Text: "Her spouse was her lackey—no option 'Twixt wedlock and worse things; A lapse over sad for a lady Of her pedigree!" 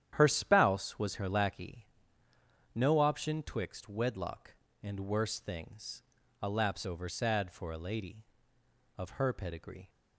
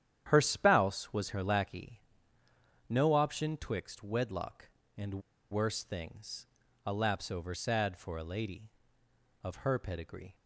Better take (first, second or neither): first